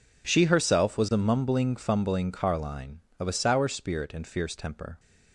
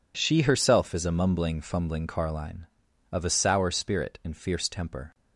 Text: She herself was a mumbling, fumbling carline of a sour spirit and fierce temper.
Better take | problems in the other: first | says "is" for "was"; at 0.9 s

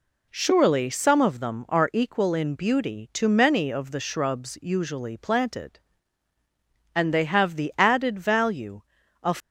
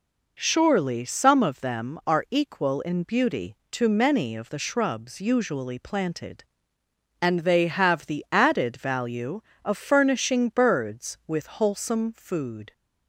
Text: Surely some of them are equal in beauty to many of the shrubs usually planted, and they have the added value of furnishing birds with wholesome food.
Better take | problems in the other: second | stops before "furnishing birds with wholesome food"; at 9.3 s

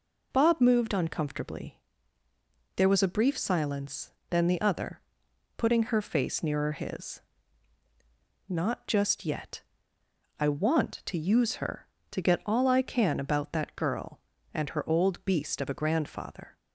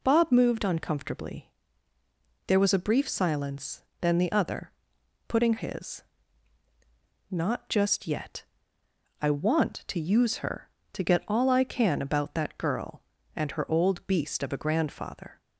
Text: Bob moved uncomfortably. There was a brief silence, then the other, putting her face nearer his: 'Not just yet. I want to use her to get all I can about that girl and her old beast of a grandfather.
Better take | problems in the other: first | skips "her face nearer"; at 5.5 s

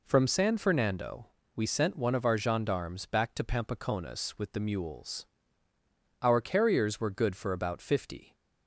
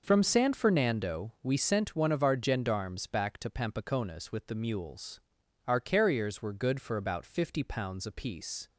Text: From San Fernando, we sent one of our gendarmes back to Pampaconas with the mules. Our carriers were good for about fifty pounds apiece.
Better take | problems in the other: second | stops before "pounds apiece"; at 8.3 s

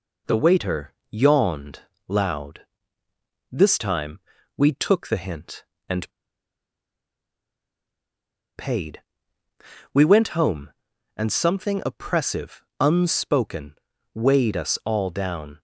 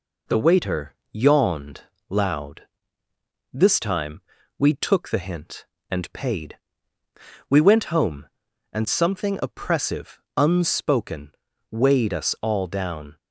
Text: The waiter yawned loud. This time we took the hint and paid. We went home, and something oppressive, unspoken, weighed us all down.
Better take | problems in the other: second | pauses between "waiter" and "yawned"; slight; at 0.9 s; 0.20 s long; slight in the second // pauses between "yawned" and "loud"; slight; at 1.8 s; 0.26 s long; slight in the second // pauses between "time" and "we"; slight; at 4.2 s; 0.36 s long; slight in the second // pauses between "and" and "paid"; strong; at 6.1 s; 2.4 s long

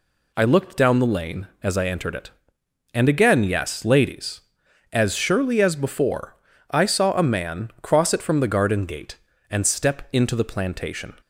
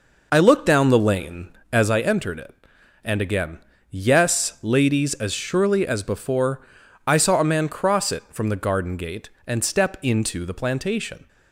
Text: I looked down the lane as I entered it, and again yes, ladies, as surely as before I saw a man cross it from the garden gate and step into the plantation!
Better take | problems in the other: first | starts louder than the rest; noticeable; until 2.0 s; 5 dB // pauses between "again" and "yes"; slight; at 3.5 s; 0.32 s long // pauses between "before" and "I"; at 6.6 s; 0.40 s long; slight in the first

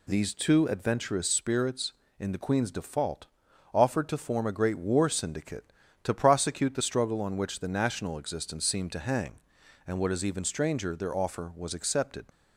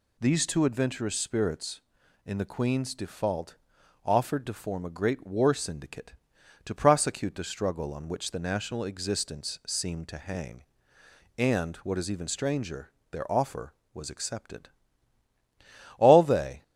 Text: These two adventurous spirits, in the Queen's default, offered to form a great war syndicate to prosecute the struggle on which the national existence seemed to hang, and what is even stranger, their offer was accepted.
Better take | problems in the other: first | goes on to say "All they"; noticeable; from 15.9 s on; 0.64 s long

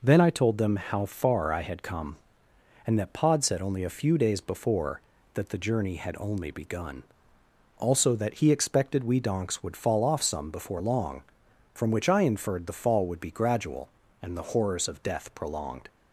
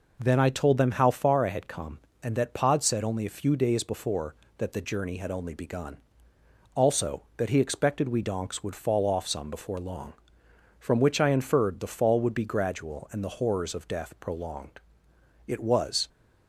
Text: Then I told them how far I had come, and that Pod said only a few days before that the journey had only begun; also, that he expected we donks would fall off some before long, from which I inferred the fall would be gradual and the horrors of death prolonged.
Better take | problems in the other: first | goes on to say "It was"; noticeable; from 15.4 s on; 0.62 s long

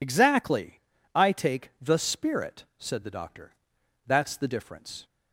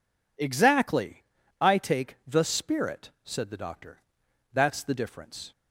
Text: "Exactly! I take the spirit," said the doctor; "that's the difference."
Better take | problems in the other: second | loses the start of "Exactly"; at 0.0 s; 60 ms

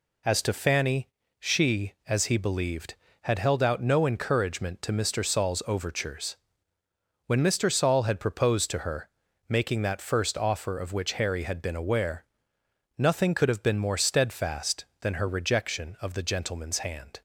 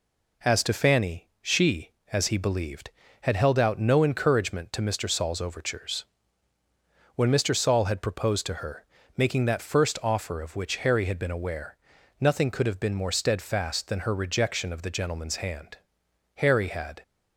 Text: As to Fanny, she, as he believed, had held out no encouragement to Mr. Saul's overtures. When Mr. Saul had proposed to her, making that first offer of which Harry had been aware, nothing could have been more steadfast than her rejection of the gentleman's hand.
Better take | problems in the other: first | goes on to say "Harry had"; noticeable; from 16.3 s on; 0.66 s long

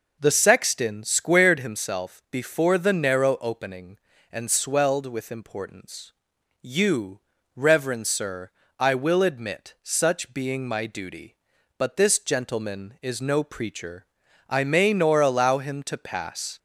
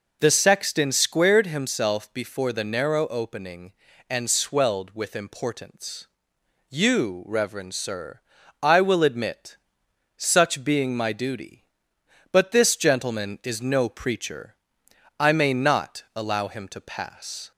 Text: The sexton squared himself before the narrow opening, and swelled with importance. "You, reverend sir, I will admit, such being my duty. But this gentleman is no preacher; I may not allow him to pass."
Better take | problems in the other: second | says "nor" for "not"; at 14.9 s

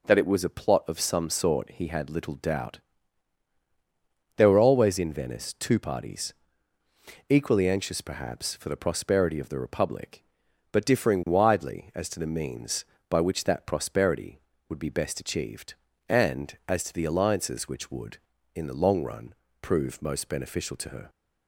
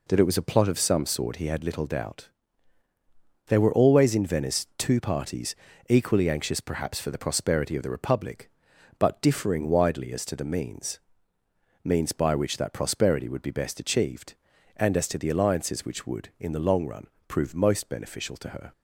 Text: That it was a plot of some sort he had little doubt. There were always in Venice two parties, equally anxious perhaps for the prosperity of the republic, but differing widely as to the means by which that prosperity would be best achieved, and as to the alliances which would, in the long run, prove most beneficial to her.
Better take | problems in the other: first | says "means" twice; at 11.8 s

